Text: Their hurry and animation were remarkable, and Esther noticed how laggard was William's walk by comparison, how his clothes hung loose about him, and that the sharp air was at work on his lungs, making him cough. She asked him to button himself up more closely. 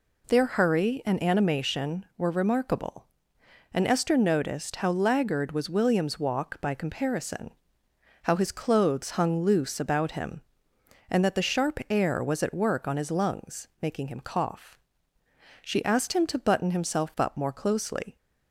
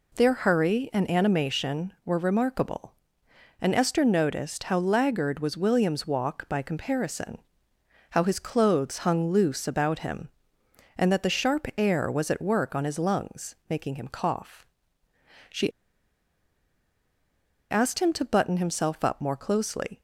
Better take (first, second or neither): first